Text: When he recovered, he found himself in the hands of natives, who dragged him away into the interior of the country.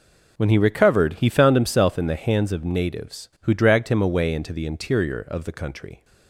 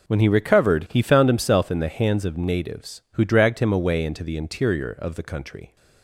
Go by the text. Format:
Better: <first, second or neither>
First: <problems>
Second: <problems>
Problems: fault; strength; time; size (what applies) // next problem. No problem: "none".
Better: neither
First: none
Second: none